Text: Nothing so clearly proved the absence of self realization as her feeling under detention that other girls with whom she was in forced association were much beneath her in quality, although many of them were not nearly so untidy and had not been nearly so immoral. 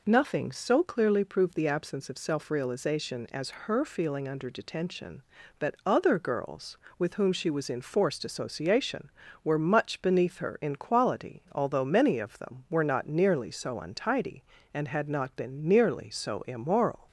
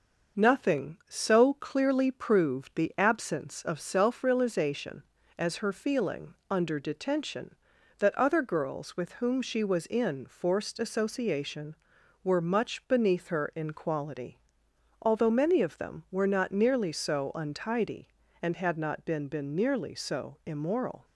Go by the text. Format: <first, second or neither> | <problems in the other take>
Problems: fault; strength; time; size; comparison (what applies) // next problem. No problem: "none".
first | starts louder than the rest; noticeable; until 1.4 s; 6 dB // says "been" twice; at 19.2 s